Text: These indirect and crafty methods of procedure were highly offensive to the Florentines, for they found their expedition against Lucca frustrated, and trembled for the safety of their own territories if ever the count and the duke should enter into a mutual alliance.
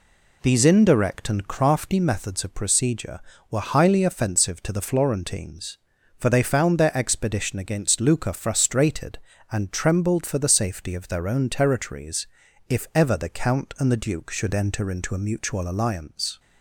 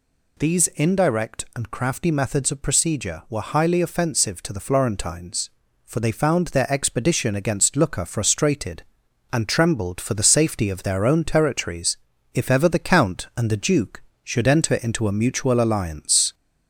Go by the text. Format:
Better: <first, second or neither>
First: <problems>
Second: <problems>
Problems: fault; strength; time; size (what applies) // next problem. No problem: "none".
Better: first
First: pauses between "territories" and "if"; at 12.2 s; 0.42 s long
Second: gets louder; slight; throughout; 2 dB // pauses between "territories" and "if"; slight; at 11.9 s; 0.36 s long